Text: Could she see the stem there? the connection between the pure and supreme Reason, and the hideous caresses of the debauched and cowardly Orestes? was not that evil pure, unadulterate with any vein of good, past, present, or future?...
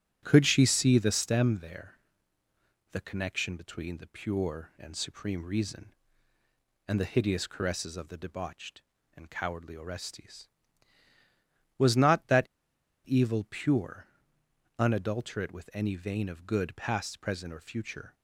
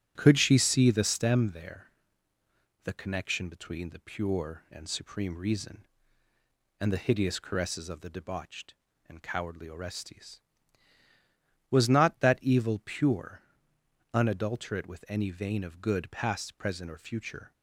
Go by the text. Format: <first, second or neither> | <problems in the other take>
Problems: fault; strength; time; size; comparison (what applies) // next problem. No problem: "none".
second | starts louder than the rest; strong; until 1.2 s; 9.5 dB; strong in the second // pauses between "that" and "evil"; noticeable; at 12.4 s; 0.59 s long